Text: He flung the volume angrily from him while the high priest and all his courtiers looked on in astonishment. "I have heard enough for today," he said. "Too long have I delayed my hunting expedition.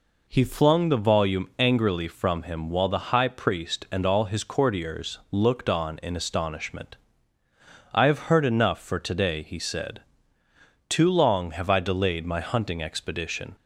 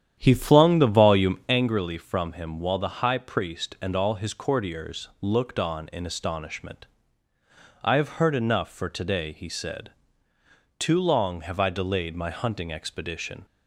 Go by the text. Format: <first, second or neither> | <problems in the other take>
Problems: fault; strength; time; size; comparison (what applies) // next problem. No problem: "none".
first | starts louder than the rest; strong; until 1.6 s; 9.5 dB